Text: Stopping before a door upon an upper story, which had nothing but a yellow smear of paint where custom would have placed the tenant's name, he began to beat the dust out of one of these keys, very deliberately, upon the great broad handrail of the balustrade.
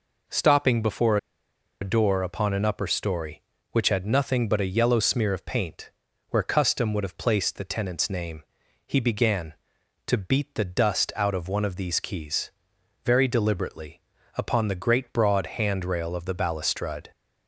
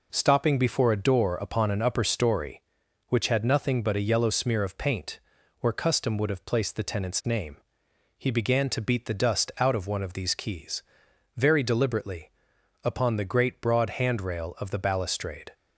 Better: second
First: pauses between "before" and "a"; noticeable; at 1.1 s; 0.64 s long // pauses between "paint" and "where"; at 5.9 s; 0.40 s long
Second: pauses between "paint" and "where"; at 5.1 s; 0.40 s long

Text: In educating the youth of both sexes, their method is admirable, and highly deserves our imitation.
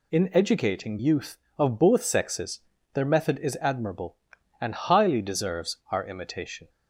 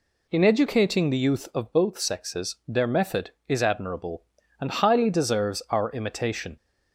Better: second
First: skips "the"; at 0.9 s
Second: none

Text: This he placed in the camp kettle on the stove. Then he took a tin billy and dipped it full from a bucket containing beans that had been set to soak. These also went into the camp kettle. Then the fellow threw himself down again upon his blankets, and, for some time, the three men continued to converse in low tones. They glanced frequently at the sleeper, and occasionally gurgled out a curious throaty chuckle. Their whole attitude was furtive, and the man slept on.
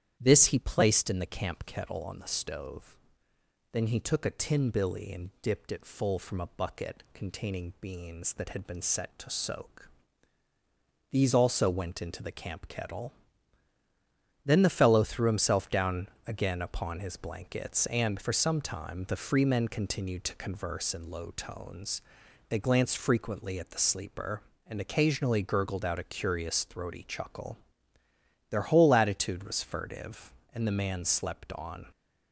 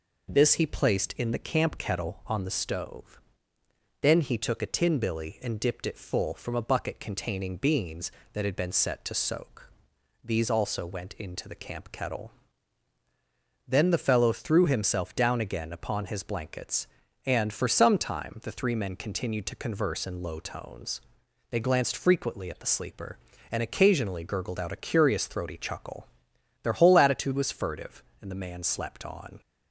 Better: second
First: starts louder than the rest; strong; until 1.2 s; 10 dB // pauses between "down" and "again"; slight; at 16.0 s; 0.18 s long // says "free" for "three"; at 19.1 s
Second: none

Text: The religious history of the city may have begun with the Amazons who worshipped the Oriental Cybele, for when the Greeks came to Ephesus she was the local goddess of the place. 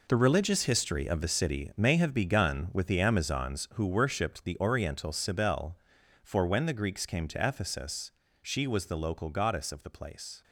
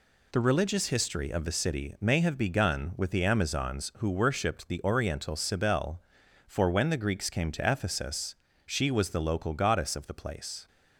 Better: second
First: gets quieter; strong; throughout; 11.5 dB // pauses between "Ephesus" and "she"; slight; at 8.1 s; 0.30 s long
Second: pauses between "Ephesus" and "she"; slight; at 8.3 s; 0.30 s long

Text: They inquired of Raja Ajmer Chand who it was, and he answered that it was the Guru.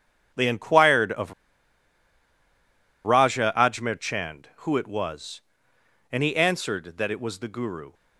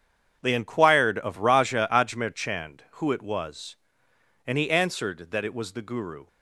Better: second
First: starts louder than the rest; strong; until 3.0 s; 8 dB // pauses between "of" and "Raja"; strong; at 1.3 s; 1.7 s long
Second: starts louder than the rest; strong; until 1.4 s; 8 dB

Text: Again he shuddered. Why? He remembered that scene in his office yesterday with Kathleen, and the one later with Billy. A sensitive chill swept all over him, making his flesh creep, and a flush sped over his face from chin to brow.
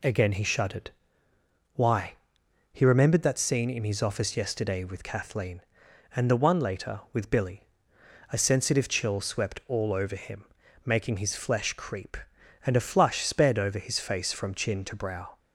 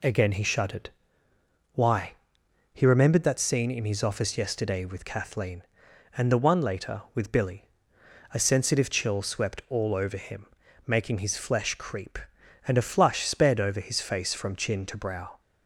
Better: neither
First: none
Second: none

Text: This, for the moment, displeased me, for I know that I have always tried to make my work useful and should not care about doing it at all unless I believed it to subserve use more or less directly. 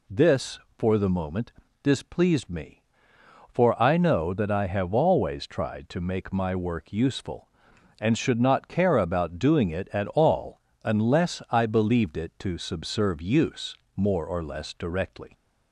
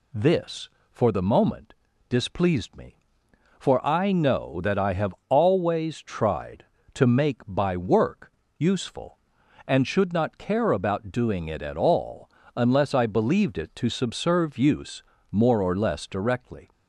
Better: first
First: pauses between "all" and "unless"; slight; at 10.5 s; 0.24 s long // pauses between "use" and "more"; slight; at 13.7 s; 0.20 s long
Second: pauses between "have" and "always"; slight; at 5.1 s; 0.16 s long // says "by" for "my"; at 7.4 s // pauses between "work" and "useful"; slight; at 8.3 s; 0.26 s long // pauses between "all" and "unless"; slight; at 12.2 s; 0.26 s long // pauses between "use" and "more"; slight; at 15.0 s; 0.28 s long

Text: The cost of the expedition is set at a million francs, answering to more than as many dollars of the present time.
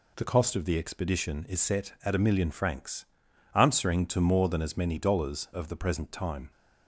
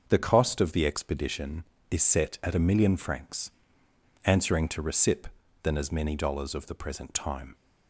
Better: first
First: none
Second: starts louder than the rest; until 1.0 s; 6 dB // says "recip" for "more"; at 4.8 s

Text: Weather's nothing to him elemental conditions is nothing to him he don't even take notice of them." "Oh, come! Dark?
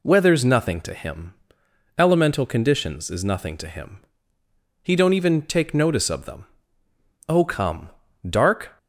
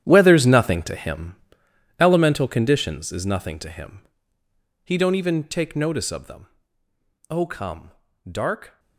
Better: first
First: pauses between "him" and "elemental"; noticeable; at 1.3 s; 0.66 s long // pauses between "him" and "he"; noticeable; at 3.9 s; 0.84 s long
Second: gets quieter; strong; throughout; 14.5 dB // pauses between "him" and "elemental"; noticeable; at 1.3 s; 0.66 s long // pauses between "him" and "he"; noticeable; at 4.0 s; 0.84 s long

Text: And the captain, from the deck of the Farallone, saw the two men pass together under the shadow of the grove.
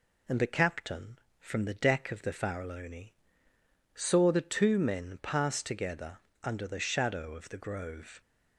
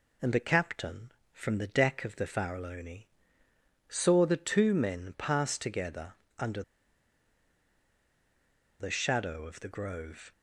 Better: first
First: pauses between "together" and "under"; slight; at 6.1 s; 0.26 s long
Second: pauses between "together" and "under"; slight; at 6.1 s; 0.26 s long // pauses between "under" and "the"; strong; at 6.6 s; 2.1 s long

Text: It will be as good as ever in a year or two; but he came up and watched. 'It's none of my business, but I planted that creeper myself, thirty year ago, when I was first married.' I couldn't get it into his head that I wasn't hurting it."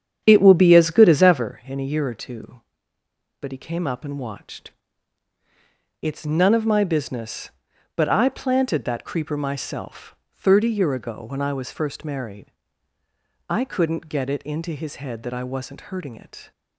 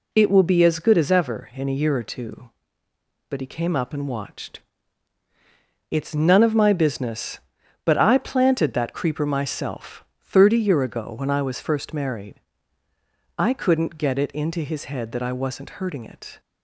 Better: second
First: starts louder than the rest; strong; until 1.5 s; 9 dB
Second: none

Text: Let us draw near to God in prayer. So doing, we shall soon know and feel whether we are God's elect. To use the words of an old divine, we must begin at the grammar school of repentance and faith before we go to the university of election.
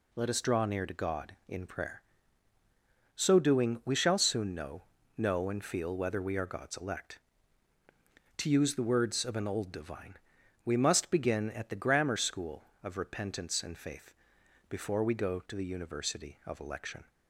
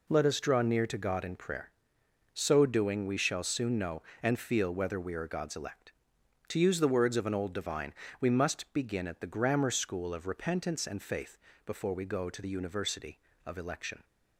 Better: second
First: says "know" twice; at 5.1 s // pauses between "faith" and "before"; noticeable; at 14.1 s; 0.56 s long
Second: pauses between "faith" and "before"; slight; at 11.3 s; 0.28 s long

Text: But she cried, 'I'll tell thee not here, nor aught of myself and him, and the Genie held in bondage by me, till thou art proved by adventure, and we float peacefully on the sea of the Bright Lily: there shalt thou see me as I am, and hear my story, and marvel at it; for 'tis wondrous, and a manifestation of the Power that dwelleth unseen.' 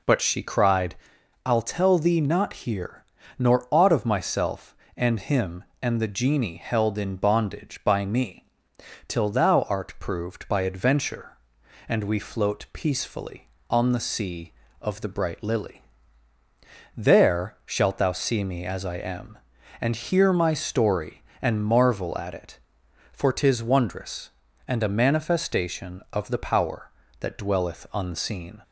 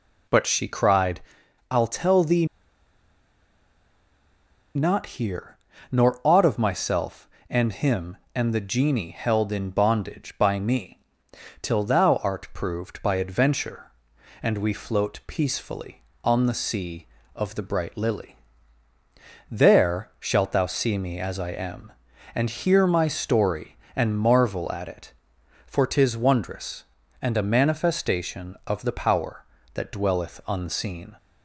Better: first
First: none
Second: pauses between "thee" and "not"; strong; at 2.4 s; 2.3 s long

